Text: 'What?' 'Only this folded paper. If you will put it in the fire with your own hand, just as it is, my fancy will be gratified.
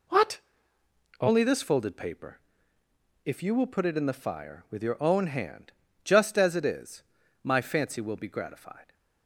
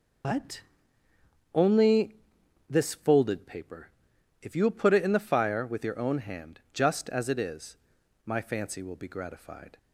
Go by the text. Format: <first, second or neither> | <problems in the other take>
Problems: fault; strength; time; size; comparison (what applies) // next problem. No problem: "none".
first | loses the start of "What"; at 0.2 s; 125 ms // pauses between "Only" and "this"; noticeable; at 2.1 s; 0.52 s long